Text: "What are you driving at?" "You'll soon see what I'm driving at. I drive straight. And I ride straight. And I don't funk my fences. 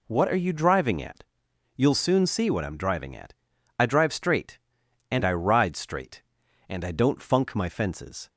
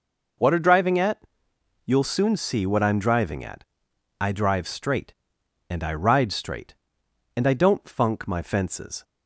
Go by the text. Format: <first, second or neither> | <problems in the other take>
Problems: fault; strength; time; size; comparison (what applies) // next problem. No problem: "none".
first | skips "you"; at 0.5 s